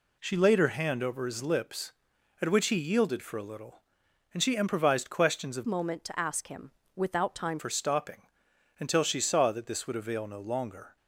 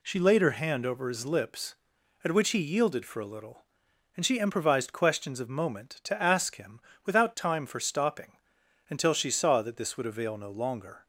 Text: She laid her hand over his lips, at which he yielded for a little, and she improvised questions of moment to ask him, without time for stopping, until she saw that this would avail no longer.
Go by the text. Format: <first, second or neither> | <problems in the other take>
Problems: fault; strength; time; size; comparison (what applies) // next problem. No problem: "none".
second | changes voice from "moment" to "time"; from 5.6 to 7.5 s; 1.9 s long